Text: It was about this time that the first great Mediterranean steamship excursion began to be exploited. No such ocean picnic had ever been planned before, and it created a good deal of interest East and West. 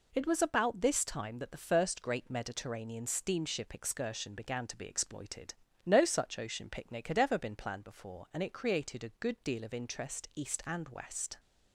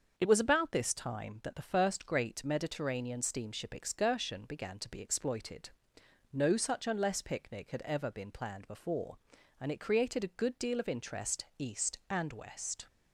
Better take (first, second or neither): first